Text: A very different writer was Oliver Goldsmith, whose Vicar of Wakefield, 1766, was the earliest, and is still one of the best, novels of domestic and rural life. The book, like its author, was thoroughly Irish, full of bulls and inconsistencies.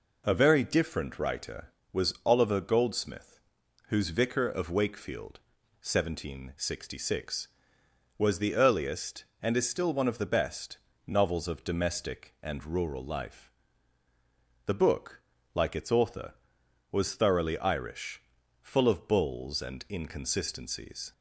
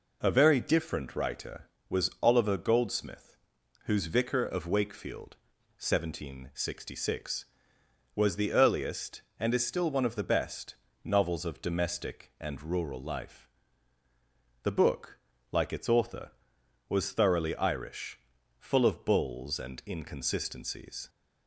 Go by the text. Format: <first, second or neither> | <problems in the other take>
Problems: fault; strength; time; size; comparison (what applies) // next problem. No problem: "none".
neither | none